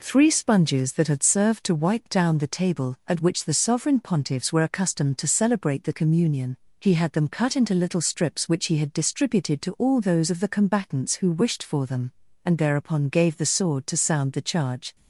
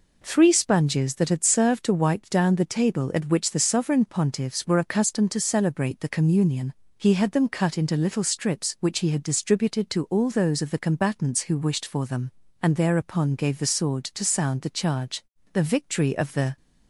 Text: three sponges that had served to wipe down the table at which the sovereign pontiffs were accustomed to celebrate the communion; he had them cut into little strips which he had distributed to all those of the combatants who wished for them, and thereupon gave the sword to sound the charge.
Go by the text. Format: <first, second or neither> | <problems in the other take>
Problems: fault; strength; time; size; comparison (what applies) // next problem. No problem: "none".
first | goes on to say "The victory of the"; noticeable; from 15.5 s on; 1.0 s long